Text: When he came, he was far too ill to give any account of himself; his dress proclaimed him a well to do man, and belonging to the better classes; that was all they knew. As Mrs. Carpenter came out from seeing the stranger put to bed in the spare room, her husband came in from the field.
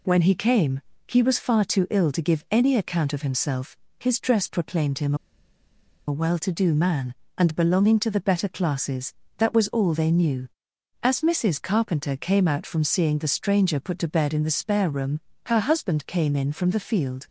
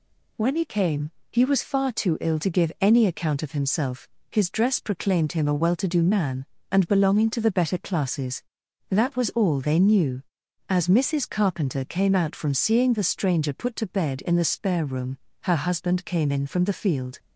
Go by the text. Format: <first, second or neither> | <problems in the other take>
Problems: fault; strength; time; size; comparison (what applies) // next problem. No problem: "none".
second | pauses between "him" and "a"; noticeable; at 5.1 s; 0.91 s long